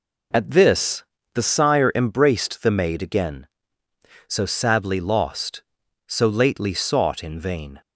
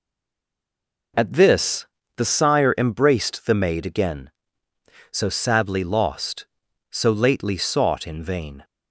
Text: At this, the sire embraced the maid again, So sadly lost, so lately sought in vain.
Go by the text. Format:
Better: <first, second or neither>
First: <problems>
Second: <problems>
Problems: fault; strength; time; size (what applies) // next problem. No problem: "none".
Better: first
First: none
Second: stays silent before the first word; until 1.1 s; 1.1 s long